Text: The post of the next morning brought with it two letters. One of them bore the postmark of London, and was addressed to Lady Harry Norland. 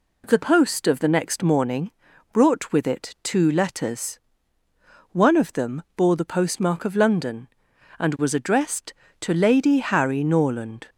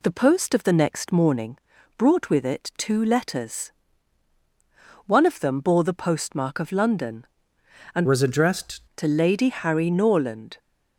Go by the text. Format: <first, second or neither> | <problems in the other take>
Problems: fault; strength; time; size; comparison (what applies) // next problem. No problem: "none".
first | pauses between "morning" and "brought"; at 1.5 s; 0.38 s long; also in the first // changes voice from "was" to "addressed"; from 8.0 to 8.8 s; 0.8 s long